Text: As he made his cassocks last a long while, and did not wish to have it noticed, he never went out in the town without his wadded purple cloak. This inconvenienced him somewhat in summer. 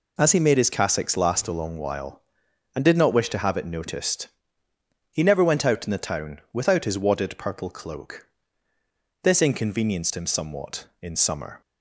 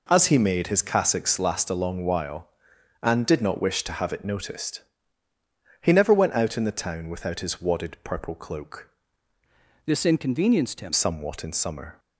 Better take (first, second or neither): first